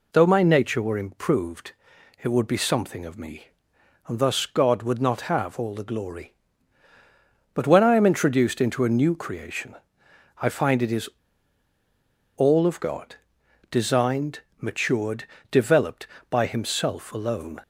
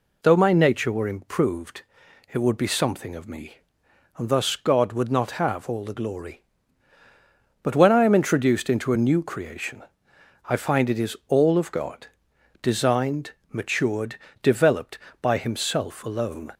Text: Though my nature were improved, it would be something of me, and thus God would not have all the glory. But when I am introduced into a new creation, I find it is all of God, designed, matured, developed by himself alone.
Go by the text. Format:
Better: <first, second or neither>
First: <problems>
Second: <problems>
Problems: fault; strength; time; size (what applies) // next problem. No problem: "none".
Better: second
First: pauses between "is" and "all"; strong; at 11.0 s; 1.2 s long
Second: none